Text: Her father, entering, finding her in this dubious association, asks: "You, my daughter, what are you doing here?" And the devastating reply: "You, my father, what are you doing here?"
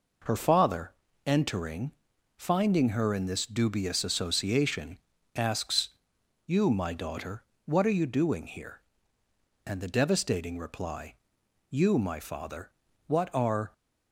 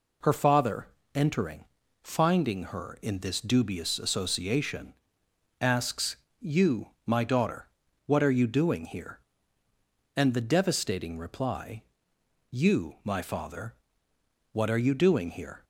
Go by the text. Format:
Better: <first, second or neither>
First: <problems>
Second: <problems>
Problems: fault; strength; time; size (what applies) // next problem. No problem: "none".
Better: second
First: stops before "you doing here"; at 13.7 s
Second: none